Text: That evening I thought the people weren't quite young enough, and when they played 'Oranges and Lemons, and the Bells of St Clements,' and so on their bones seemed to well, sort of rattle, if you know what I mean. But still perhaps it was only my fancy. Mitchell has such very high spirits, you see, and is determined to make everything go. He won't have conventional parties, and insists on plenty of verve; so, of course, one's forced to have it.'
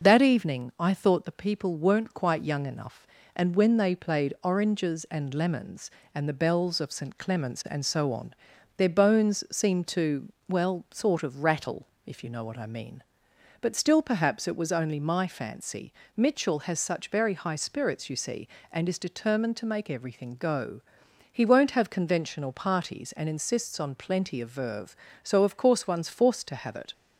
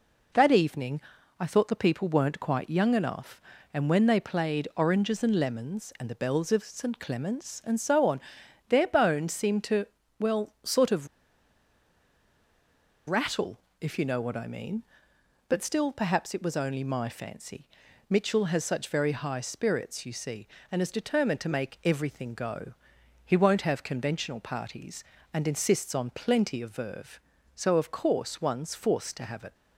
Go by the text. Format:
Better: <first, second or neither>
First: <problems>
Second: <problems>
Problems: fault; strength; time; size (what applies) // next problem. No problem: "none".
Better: first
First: pauses between "on" and "their"; at 8.3 s; 0.42 s long // pauses between "to" and "well"; slight; at 10.2 s; 0.16 s long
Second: pauses between "evening" and "I"; at 1.0 s; 0.38 s long // pauses between "on" and "their"; noticeable; at 8.1 s; 0.52 s long // pauses between "to" and "well"; slight; at 9.8 s; 0.34 s long // pauses between "of" and "rattle"; strong; at 11.0 s; 2.0 s long